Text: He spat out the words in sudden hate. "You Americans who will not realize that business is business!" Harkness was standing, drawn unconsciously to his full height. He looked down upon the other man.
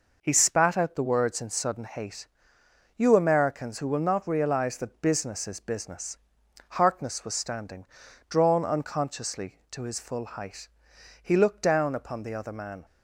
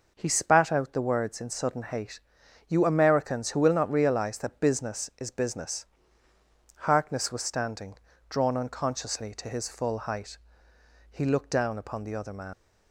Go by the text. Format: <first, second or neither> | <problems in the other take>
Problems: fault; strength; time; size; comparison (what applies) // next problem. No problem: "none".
first | leaves "man" unfinished; at 12.5 s; 105 ms